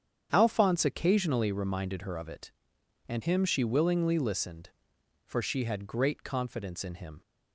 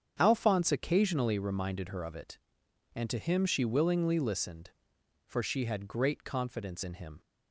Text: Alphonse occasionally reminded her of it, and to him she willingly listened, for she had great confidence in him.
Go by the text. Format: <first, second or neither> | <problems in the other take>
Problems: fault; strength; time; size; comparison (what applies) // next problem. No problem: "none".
second | starts louder than the rest; strong; until 1.3 s; 8.5 dB; strong in the second // skips "to"; at 3.2 s